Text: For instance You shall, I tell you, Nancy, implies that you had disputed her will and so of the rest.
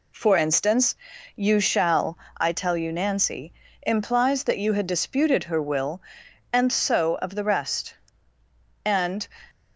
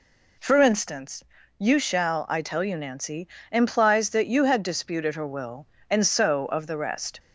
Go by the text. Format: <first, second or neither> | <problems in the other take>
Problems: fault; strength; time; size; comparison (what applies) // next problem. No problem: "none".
second | pauses between "instance" and "You"; at 0.9 s; 0.42 s long; slight in the second // goes on to say "And"; slight; from 8.8 s on; 0.42 s long